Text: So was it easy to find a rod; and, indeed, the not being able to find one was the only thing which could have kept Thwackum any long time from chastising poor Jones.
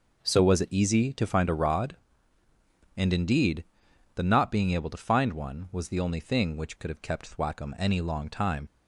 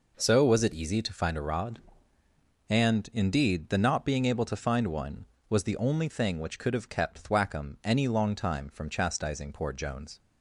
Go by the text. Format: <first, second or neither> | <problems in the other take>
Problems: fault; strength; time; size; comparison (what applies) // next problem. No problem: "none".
second | stops before "from chastising poor Jones"; at 8.6 s